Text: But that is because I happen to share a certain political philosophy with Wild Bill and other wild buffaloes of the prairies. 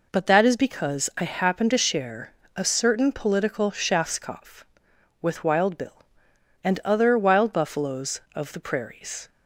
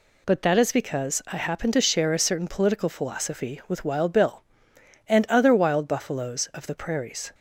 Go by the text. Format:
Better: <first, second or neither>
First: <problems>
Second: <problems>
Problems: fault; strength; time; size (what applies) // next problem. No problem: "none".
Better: second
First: pauses between "share" and "a"; slight; at 2.3 s; 0.22 s long // says "schafskopf" for "philosophy"; at 3.7 s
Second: none